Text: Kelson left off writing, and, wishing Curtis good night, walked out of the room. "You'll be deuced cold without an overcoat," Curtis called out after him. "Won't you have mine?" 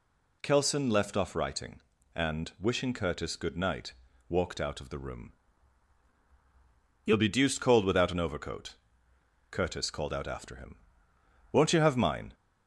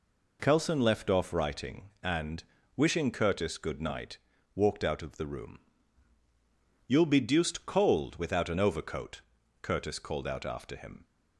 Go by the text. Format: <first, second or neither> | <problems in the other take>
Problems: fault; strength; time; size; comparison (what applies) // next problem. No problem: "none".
first | stops before "Won't you have mine"; at 11.0 s